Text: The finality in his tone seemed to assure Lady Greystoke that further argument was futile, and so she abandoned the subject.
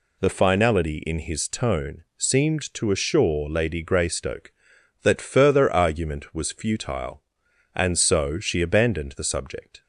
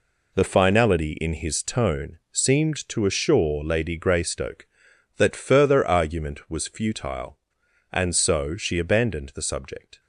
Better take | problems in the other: first | gets quieter; strong; throughout; 9 dB // pauses between "tone" and "seemed"; slight; at 2.1 s; 0.16 s long; slight in the first

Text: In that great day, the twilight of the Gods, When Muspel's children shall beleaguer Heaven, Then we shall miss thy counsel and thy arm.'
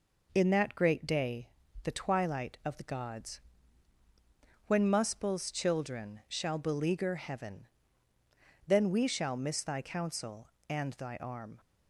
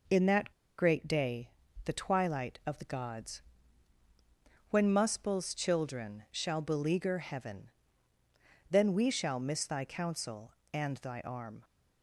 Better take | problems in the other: first | pauses between "that" and "great"; slight; at 0.5 s; 0.25 s long

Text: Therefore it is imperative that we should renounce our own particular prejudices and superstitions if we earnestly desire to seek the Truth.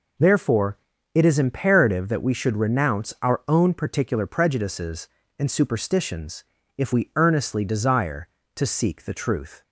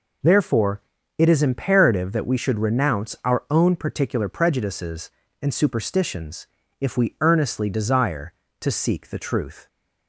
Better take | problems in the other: neither | pauses between "Therefore" and "it"; slight; the same in both // pauses between "superstitions" and "if"; slight; the same in both

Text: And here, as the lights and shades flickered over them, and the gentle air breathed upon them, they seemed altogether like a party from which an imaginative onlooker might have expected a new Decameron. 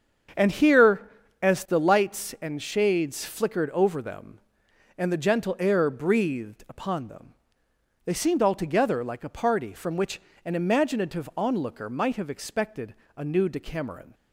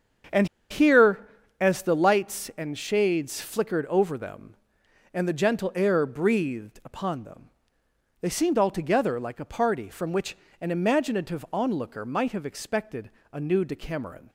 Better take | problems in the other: first | starts louder than the rest; until 1.8 s; 7 dB; strong in the first // pauses between "And" and "here"; slight; at 0.4 s; 0.23 s long // pauses between "which" and "an"; slight; at 10.3 s; 0.24 s long; slight in the first // pauses between "expected" and "a"; slight; at 13.0 s; 0.22 s long; slight in the first

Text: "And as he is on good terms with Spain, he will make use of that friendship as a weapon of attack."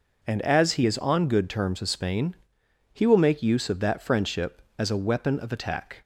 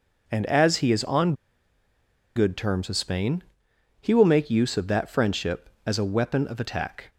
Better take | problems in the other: first | pauses between "on" and "good"; at 1.3 s; 1.0 s long

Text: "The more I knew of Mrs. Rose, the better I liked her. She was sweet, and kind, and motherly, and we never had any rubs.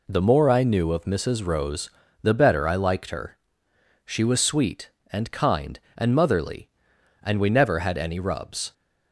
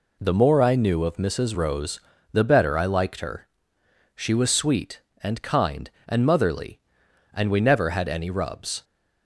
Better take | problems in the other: neither | none

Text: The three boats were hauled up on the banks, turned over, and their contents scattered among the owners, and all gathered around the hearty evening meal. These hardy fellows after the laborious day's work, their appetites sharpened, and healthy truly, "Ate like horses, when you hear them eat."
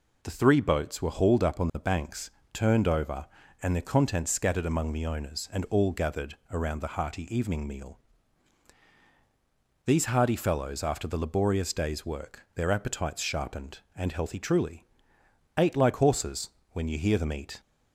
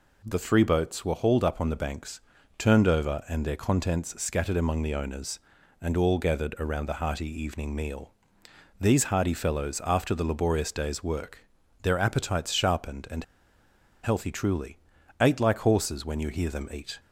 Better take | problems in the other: first | pauses between "and" and "healthy"; noticeable; at 13.2 s; 0.79 s long

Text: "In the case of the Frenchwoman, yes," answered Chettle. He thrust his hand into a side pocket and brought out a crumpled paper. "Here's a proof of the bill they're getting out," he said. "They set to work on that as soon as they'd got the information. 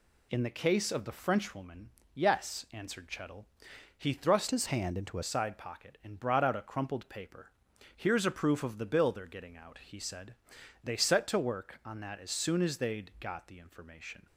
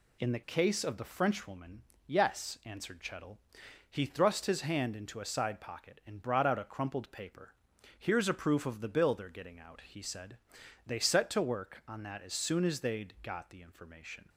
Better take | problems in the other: second | changes voice from "his" to "a"; from 4.5 to 5.2 s; 0.7 s long

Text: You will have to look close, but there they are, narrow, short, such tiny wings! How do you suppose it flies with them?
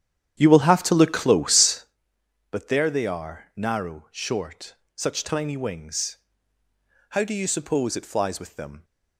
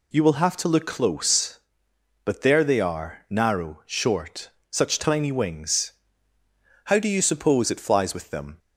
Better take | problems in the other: second | starts louder than the rest; strong; until 2.0 s; 9.5 dB

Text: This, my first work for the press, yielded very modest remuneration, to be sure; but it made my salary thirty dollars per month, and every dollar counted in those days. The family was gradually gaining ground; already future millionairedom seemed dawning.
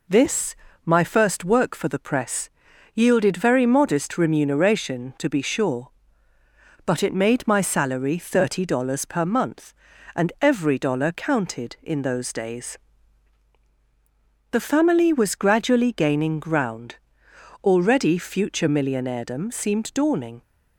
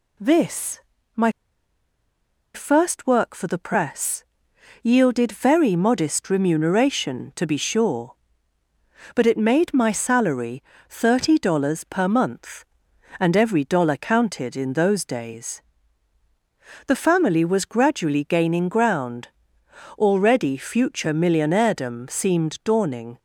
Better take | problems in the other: first | pauses between "my" and "first"; at 1.3 s; 1.2 s long // pauses between "salary" and "thirty"; slight; at 10.6 s; 0.26 s long

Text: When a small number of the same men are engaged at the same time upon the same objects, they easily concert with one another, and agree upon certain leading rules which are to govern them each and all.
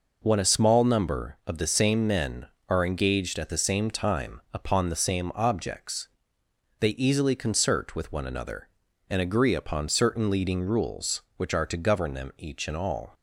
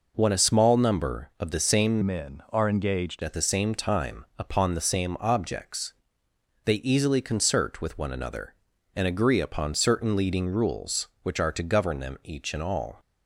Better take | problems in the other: first | changes voice from "men" to "engaged"; from 2.0 to 3.2 s; 1.2 s long

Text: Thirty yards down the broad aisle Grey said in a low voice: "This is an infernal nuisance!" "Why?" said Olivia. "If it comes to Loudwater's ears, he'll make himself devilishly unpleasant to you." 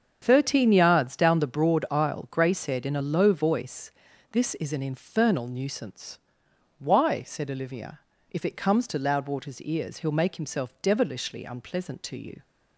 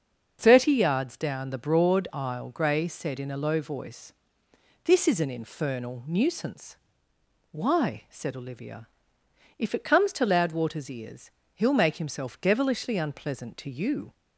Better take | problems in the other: second | starts louder than the rest; strong; until 1.2 s; 7.5 dB; also in the second // says "Thirteen" for "Thirty"; at 0.2 s

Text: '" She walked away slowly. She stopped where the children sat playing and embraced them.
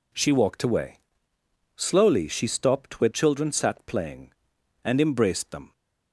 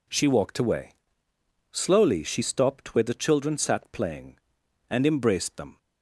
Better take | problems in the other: second | pauses between "away" and "slowly"; noticeable; at 0.9 s; 0.76 s long; noticeable in the second // skips "the"; at 3.0 s

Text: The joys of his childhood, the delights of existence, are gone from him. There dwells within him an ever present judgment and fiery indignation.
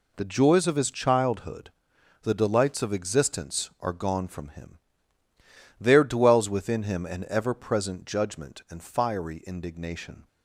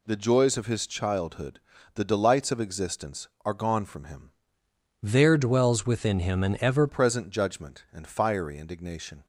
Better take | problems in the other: first | changes voice from "There" to "ever"; from 5.0 to 6.8 s; 1.8 s long

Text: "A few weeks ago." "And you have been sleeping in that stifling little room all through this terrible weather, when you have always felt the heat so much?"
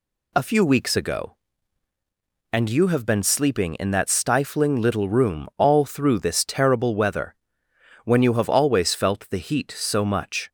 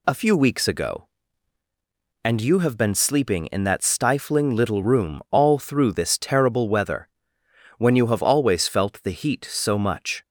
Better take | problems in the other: neither | none

